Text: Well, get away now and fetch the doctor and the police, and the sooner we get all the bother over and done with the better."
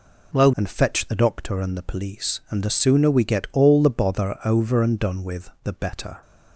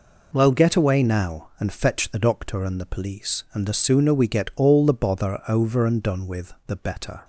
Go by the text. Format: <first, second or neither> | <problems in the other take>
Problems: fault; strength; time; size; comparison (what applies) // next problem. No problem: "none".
second | skips "get away now"; at 0.5 s // pauses between "with" and "the"; slight; at 5.4 s; 0.16 s long; slight in the second